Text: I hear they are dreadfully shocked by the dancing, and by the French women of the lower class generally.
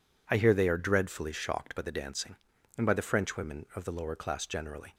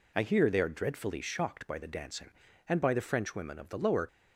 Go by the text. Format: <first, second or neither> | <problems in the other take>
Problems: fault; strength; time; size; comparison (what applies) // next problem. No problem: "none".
first | stops before "class generally"; at 4.0 s